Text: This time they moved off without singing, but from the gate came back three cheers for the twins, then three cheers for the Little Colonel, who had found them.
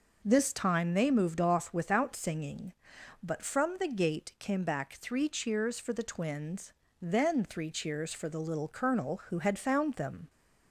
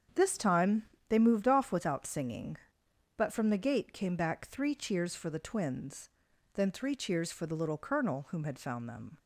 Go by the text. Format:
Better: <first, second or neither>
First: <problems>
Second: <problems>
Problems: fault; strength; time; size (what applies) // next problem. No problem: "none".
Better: first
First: none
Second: starts louder than the rest; strong; until 1.4 s; 7.5 dB // pauses between "time" and "they"; slight; at 0.8 s; 0.24 s long // says "whom" for "who"; at 8.2 s